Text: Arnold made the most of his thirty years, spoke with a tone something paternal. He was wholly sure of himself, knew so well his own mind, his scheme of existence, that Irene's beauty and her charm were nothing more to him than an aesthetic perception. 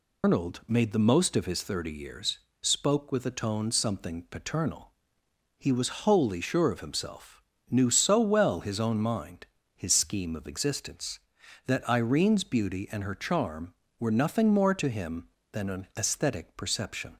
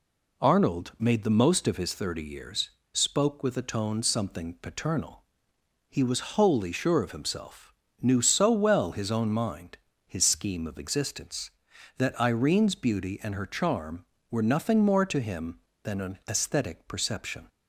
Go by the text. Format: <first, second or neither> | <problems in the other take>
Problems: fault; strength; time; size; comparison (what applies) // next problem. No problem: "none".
second | loses the start of "Arnold"; at 0.2 s; 150 ms